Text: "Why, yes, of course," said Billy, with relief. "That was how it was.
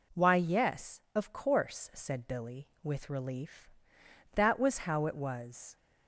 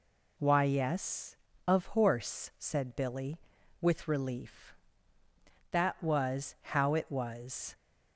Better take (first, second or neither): first